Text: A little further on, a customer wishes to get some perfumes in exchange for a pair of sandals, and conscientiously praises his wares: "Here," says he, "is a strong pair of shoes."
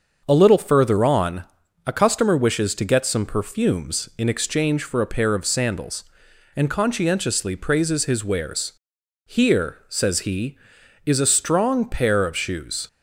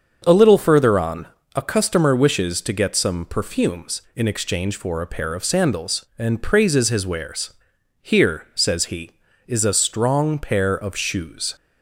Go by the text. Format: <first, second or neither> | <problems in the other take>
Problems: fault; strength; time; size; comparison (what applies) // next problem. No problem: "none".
first | starts louder than the rest; until 1.2 s; 7 dB; also in the first // skips "conscientiously"; at 6.4 s